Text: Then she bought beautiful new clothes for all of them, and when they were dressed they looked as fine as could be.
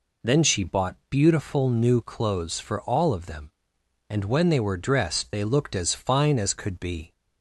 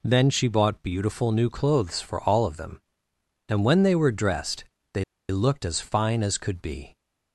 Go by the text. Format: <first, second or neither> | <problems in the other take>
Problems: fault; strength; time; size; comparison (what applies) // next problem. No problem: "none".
first | pauses between "dressed" and "they"; slight; at 4.6 s; 0.30 s long // pauses between "they" and "looked"; slight; at 5.0 s; 0.27 s long